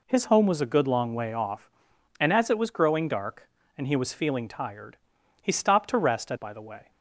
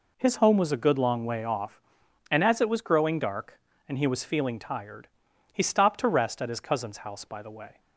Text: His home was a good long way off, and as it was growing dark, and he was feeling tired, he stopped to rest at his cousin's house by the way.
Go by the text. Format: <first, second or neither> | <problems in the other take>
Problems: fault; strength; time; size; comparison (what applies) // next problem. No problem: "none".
second | skips "his cousin's house"; at 6.3 s